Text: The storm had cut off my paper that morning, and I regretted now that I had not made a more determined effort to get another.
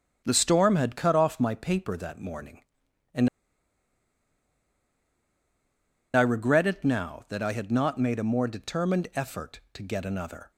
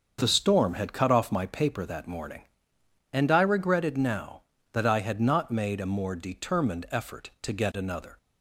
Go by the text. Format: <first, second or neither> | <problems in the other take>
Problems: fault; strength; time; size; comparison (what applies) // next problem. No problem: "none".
second | starts louder than the rest; strong; until 1.2 s; 8.5 dB; also in the second // pauses between "and" and "I"; strong; at 3.2 s; 2.8 s long